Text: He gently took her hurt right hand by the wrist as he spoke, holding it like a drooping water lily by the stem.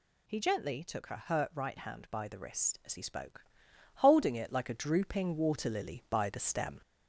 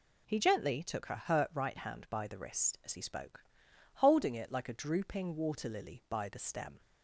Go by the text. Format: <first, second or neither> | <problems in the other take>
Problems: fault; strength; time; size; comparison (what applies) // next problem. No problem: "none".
second | gets louder; slight; throughout; 2 dB